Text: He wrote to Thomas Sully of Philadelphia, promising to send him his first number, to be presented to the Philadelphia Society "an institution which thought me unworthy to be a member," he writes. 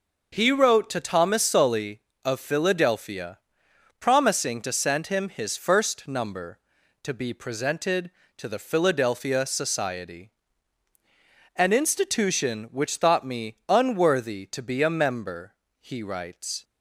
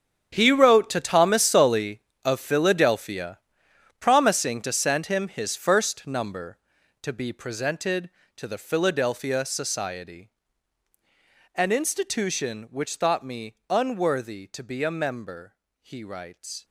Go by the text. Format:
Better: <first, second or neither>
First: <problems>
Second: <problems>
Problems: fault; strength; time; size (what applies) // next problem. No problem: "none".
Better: first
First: pauses between "Society" and "an"; at 10.3 s; 1.2 s long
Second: gets quieter; strong; throughout; 15 dB // pauses between "Society" and "an"; at 10.3 s; 1.2 s long